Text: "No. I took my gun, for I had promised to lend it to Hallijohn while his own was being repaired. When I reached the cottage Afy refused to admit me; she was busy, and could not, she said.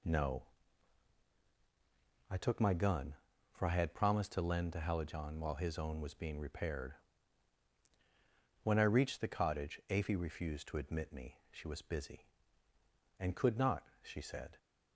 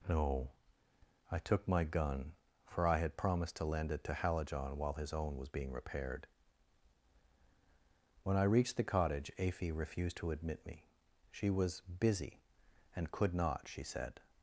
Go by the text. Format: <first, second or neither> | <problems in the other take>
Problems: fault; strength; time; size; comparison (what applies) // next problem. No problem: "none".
second | skips "it"; at 4.7 s